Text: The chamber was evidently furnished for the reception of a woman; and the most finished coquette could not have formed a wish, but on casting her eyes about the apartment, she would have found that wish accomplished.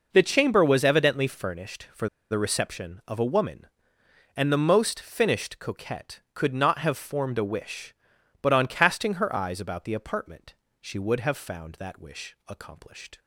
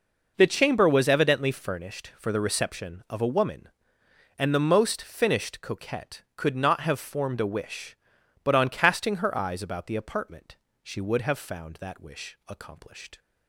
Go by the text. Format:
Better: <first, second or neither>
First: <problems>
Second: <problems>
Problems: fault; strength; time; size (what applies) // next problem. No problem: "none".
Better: second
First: pauses between "for" and "the"; slight; at 2.0 s; 0.22 s long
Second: none